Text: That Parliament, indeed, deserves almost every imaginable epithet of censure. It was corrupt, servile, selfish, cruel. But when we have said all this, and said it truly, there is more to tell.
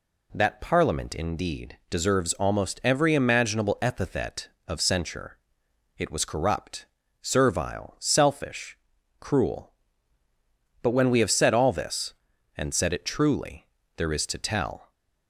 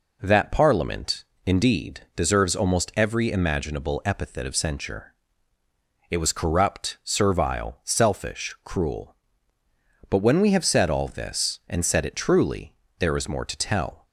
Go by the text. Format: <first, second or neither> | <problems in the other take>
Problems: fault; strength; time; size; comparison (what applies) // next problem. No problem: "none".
second | skips "more"; at 14.2 s